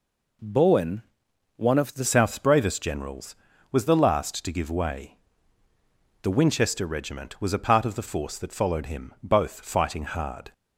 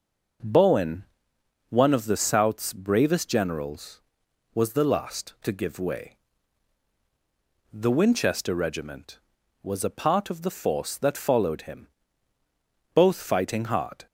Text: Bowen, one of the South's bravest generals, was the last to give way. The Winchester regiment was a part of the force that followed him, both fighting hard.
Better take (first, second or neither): second